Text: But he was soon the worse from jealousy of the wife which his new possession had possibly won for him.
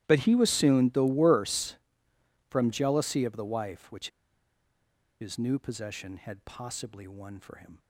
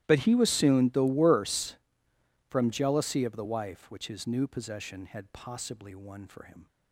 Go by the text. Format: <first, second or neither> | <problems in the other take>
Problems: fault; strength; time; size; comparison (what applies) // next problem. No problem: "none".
second | starts louder than the rest; strong; until 1.0 s; 14 dB; strong in the second // pauses between "which" and "his"; at 4.0 s; 1.1 s long